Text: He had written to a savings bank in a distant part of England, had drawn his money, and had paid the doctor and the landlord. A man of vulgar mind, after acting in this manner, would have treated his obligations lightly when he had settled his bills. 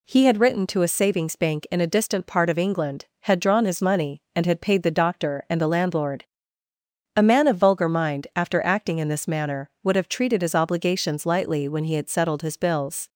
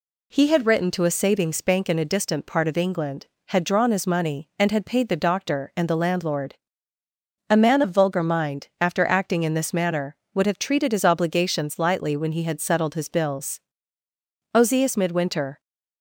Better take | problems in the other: first | goes on to say "Ozias Midwinter"; noticeable; from 14.5 s on; 1.0 s long

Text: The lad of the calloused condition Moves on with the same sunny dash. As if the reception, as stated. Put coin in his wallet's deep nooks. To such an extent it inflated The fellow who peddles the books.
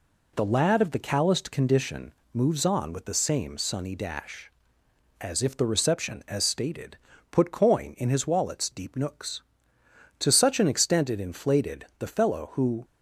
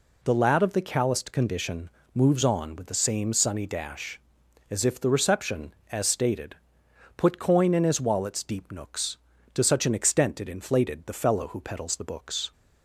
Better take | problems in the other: second | pauses between "condition" and "Moves"; slight; at 2.1 s; 0.24 s long; slight in the second // stops before "peddles the books"; at 12.8 s

